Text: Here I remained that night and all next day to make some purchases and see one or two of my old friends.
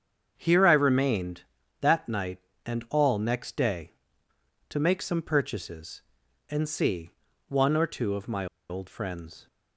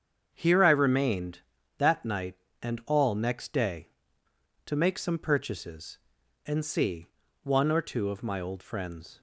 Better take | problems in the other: second | starts louder than the rest; strong; until 1.3 s; 7.5 dB; strong in the second // pauses between "see" and "one"; slight; at 7.1 s; 0.36 s long; slight in the second // pauses between "my" and "old"; slight; at 8.4 s; 0.24 s long

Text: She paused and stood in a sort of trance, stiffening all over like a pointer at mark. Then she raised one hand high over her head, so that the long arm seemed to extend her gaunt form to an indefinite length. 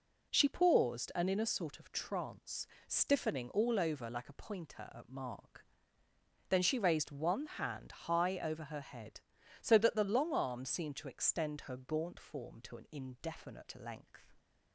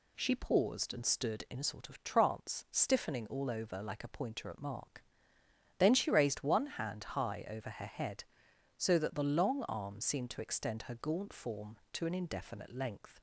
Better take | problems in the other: second | skips "stood"; at 1.2 s

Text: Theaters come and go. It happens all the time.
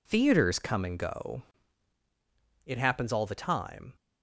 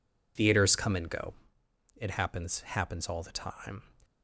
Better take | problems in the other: first | says "happens" twice; at 2.6 s

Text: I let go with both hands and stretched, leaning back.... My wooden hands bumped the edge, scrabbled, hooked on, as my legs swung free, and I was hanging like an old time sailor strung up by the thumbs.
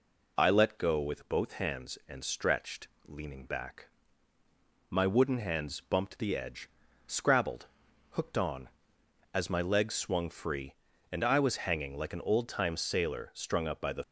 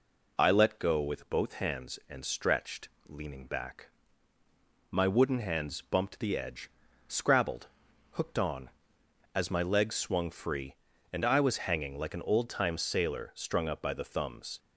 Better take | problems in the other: second | stops before "thumbs"; at 14.0 s

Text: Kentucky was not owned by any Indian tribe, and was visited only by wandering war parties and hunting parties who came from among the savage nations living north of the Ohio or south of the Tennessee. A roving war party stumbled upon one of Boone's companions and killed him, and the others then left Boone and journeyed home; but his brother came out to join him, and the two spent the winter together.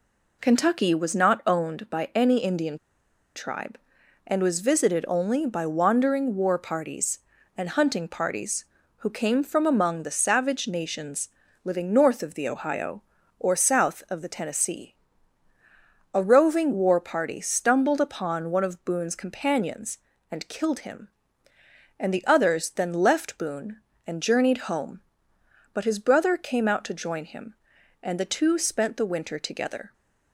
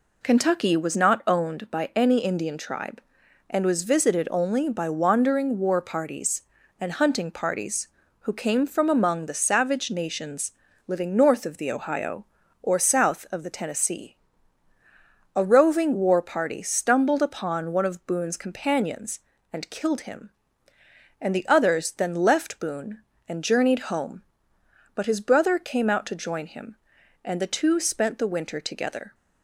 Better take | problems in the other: second | pauses between "Indian" and "tribe"; noticeable; at 2.7 s; 0.59 s long // pauses between "nations" and "living"; slight; at 11.2 s; 0.36 s long; slight in the second

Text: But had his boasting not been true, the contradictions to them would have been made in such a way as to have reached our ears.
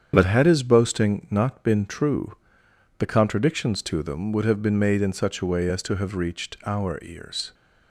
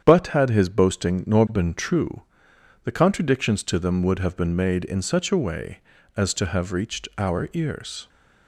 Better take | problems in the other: first | starts louder than the rest; strong; until 1.0 s; 8.5 dB; strong in the first // says "nor" for "not"; at 1.2 s

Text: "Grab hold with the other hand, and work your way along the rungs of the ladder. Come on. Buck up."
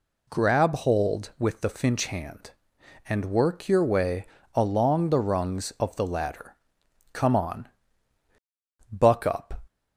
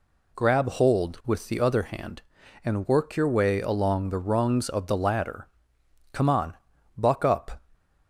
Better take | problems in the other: second | says "finch" for "other"; at 1.7 s // pauses between "way" and "along"; slight; at 4.2 s; 0.30 s long

